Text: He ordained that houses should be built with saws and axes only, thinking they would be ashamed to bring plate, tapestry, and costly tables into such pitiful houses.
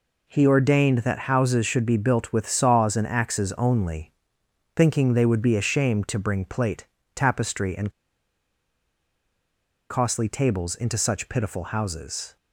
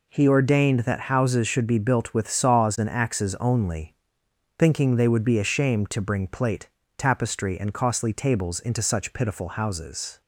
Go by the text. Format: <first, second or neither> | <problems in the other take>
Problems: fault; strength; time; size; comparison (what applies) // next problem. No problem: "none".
second | pauses between "and" and "costly"; strong; at 7.9 s; 1.9 s long